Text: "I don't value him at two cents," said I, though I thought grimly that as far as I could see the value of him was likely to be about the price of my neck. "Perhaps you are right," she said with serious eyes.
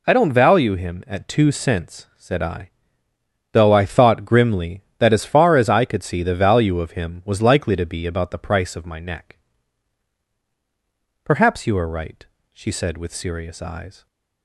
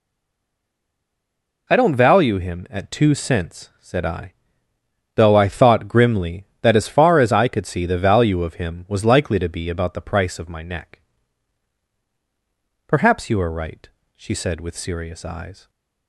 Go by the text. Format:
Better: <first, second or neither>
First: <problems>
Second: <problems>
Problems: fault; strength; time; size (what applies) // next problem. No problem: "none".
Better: first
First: none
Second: stays silent before the first word; noticeable; until 1.6 s; 1.6 s long